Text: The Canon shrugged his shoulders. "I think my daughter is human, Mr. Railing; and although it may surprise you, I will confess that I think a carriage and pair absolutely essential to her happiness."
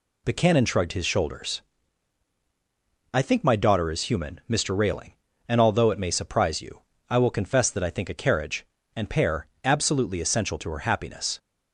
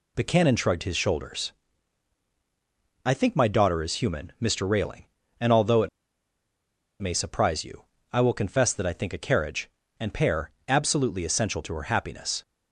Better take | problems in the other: first | pauses between "it" and "may"; at 5.8 s; 1.1 s long // pauses between "pair" and "absolutely"; slight; at 10.4 s; 0.18 s long; slight in the first

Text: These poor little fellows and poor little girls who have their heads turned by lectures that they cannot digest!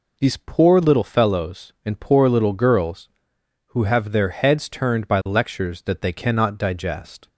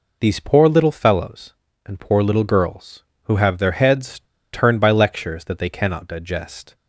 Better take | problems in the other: first | pauses between "heads" and "turned"; slight; at 4.1 s; 0.33 s long

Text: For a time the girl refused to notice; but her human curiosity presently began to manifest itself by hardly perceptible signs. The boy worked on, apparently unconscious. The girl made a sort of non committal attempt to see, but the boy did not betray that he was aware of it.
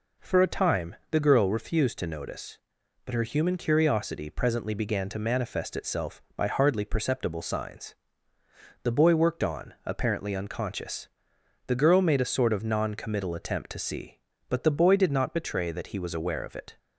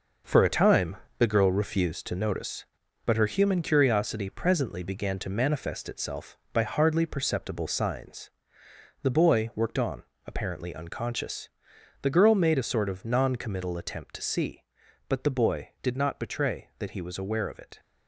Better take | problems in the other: first | gets quieter; strong; throughout; 8 dB // pauses between "time" and "the"; slight; at 0.9 s; 0.24 s long

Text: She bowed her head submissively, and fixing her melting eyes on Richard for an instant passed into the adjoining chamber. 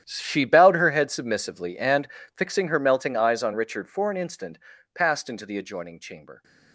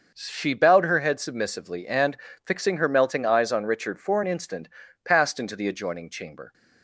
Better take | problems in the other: second | gets quieter; strong; throughout; 16.5 dB // starts louder than the rest; strong; until 1.0 s; 10.5 dB; noticeable in the second // pauses between "and" and "fixing"; slight; at 2.0 s; 0.30 s long; slight in the second // pauses between "instant" and "passed"; slight; at 4.5 s; 0.36 s long; slight in the second

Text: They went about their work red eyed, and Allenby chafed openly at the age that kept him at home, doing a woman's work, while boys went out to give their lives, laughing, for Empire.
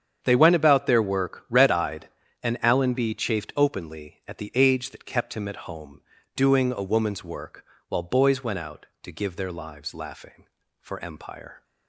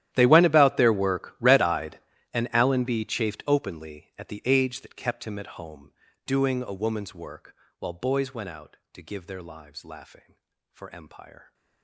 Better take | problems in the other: first | gets quieter; strong; throughout; 21.5 dB // starts louder than the rest; strong; until 1.1 s; 12 dB; strong in the first

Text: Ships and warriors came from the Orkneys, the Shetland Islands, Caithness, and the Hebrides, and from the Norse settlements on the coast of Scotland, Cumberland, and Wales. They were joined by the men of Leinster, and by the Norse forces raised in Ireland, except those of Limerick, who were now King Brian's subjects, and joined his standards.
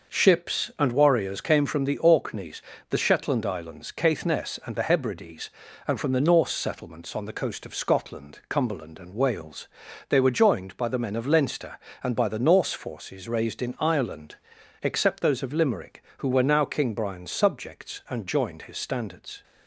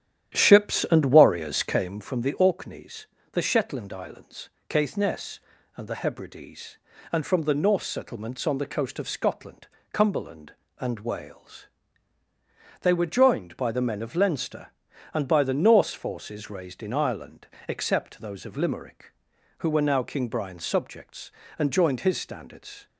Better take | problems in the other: first | starts louder than the rest; strong; until 2.0 s; 10.5 dB

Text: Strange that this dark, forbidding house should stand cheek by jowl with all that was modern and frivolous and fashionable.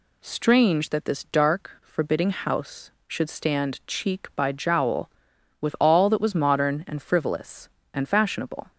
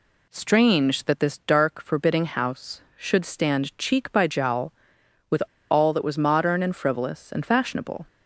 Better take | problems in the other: first | pauses between "with" and "all"; slight; at 5.4 s; 0.28 s long

